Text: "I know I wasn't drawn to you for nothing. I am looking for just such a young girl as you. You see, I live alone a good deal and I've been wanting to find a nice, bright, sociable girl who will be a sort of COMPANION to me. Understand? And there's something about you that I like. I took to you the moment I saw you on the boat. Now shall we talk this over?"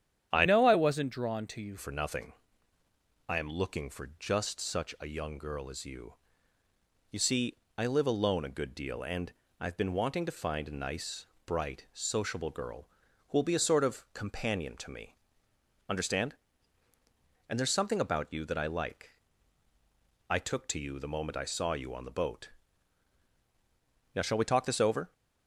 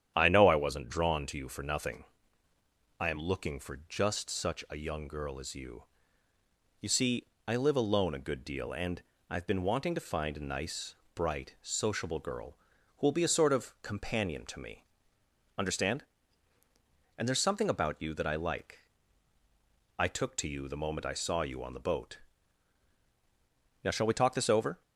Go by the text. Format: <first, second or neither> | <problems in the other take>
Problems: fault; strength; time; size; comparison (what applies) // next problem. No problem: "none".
second | starts louder than the rest; strong; until 1.3 s; 9.5 dB; strong in the second // changes voice from "know" to "you"; from 0.4 to 1.7 s; 1.3 s long // pauses between "and" and "I've"; slight; at 9.3 s; 0.28 s long; slight in the second